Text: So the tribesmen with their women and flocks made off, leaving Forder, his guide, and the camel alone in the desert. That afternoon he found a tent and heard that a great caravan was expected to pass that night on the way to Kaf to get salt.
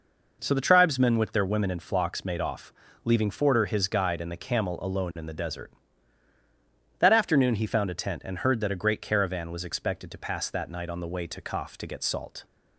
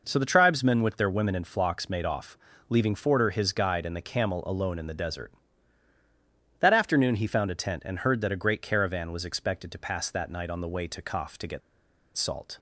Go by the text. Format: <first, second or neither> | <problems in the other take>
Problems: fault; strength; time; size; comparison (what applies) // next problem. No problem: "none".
first | pauses between "get" and "salt"; noticeable; at 11.6 s; 0.56 s long